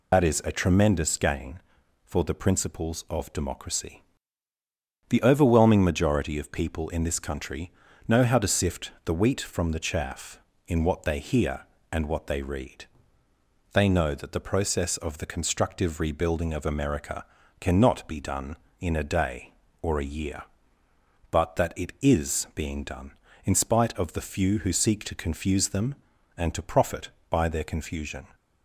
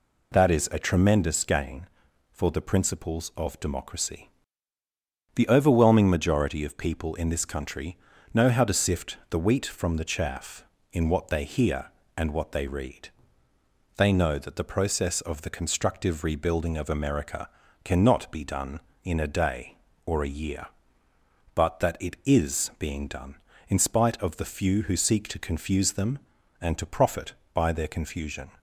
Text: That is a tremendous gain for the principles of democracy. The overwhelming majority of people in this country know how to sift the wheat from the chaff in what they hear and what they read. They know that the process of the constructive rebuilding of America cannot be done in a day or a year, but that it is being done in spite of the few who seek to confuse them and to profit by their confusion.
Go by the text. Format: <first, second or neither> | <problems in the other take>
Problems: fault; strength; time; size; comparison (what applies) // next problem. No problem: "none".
second | loses the start of "That"; at 0.1 s; 75 ms // pauses between "country" and "know"; slight; at 7.7 s; 0.36 s long; slight in the second // pauses between "America" and "cannot"; slight; at 17.2 s; 0.36 s long; slight in the second